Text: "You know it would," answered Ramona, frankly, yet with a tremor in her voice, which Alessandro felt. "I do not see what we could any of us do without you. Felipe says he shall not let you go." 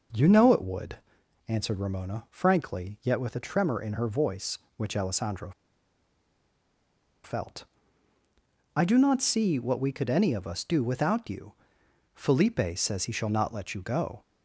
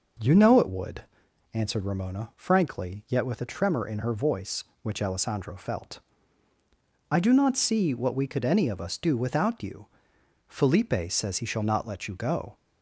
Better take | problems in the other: second | pauses between "Alessandro" and "felt"; strong; at 5.5 s; 1.7 s long

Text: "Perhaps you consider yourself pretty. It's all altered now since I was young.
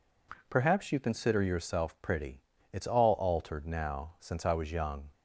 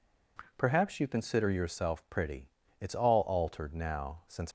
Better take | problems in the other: first | stops before "I was young"; at 4.4 s

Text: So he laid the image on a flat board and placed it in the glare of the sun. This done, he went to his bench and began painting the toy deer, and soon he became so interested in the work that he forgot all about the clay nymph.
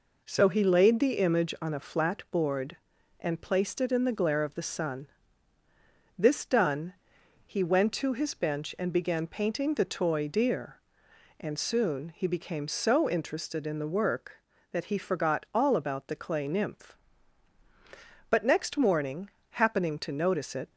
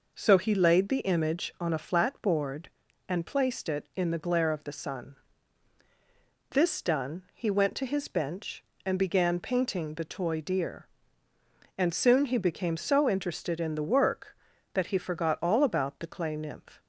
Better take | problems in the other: second | goes on to say "But next morning happening to notice it"; strong; from 18.3 s on; 2.4 s long

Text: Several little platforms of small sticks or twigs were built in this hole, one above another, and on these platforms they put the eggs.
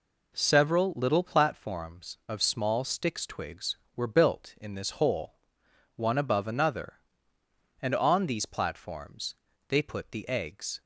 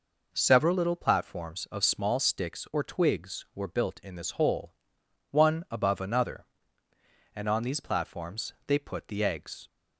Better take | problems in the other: second | skips "or"; at 3.2 s // pauses between "platforms" and "they"; slight; at 9.3 s; 0.34 s long

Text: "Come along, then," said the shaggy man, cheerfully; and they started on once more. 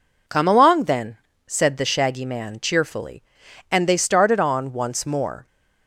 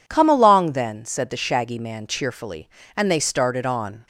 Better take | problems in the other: first | stops before "once more"; at 4.0 s

